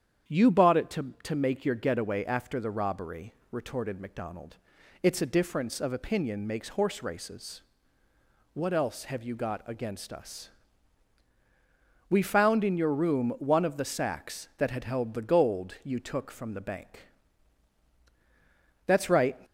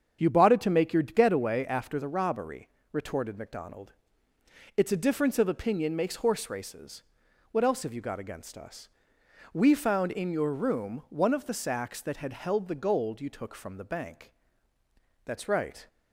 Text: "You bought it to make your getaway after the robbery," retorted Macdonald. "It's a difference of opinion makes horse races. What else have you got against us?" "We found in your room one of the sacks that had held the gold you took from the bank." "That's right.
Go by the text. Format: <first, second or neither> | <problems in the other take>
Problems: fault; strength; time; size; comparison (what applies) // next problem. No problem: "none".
second | starts louder than the rest; strong; until 1.3 s; 8.5 dB; strong in the second // says "to" twice; at 1.2 s